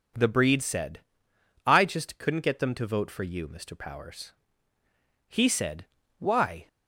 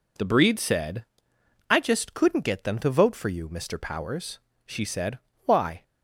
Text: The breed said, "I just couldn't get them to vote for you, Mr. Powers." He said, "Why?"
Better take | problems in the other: first | says "She" for "He"; at 4.6 s

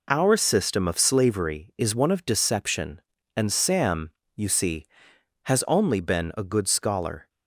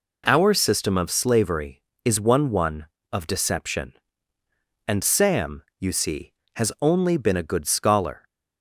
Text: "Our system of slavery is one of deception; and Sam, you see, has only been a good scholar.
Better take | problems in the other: first | says "one" twice; at 2.5 s

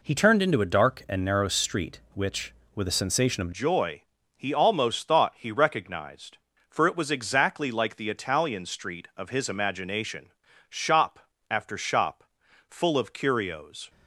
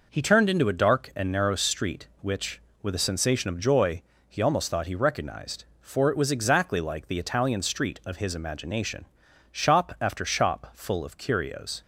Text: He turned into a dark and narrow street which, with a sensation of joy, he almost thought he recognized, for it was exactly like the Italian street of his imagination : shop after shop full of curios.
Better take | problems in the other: second | changes voice at "joy"; from 3.5 s on; 10.3 s long // pauses between "shop" and "after"; slight; at 11.1 s; 0.32 s long // pauses between "shop" and "full"; noticeable; at 12.2 s; 0.46 s long

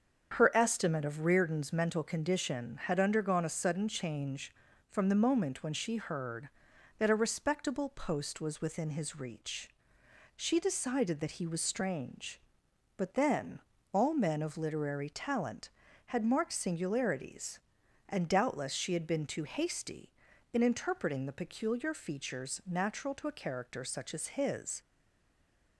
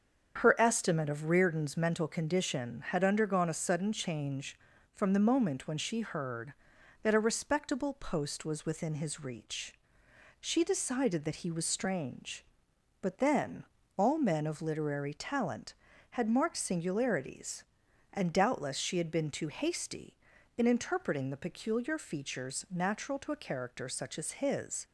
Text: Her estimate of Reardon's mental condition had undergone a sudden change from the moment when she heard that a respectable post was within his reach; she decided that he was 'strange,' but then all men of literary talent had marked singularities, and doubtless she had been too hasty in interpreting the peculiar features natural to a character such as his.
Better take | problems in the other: second | starts louder than the rest; strong; until 1.4 s; 7.5 dB; strong in the second // pauses between "then" and "all"; slight; at 13.6 s; 0.32 s long; slight in the second // stays silent after the last word; from 24.8 s on; 0.9 s long

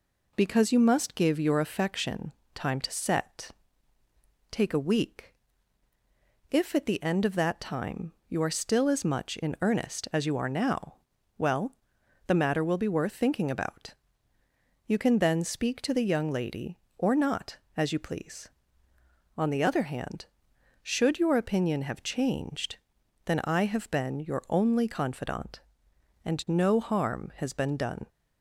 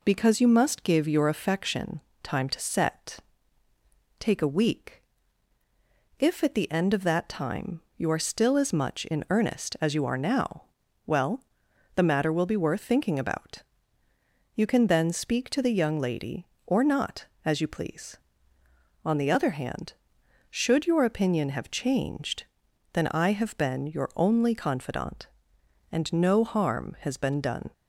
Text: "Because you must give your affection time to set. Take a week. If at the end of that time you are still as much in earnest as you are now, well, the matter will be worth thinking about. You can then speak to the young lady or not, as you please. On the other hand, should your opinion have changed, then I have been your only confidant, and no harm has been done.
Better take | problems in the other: neither | pauses between "affection" and "time"; slight; the same in both

